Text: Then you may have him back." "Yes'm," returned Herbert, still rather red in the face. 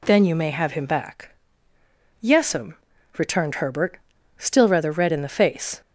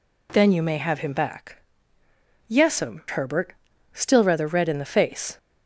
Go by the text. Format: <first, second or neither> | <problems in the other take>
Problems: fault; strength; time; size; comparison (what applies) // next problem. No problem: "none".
first | skips "returned"; at 3.0 s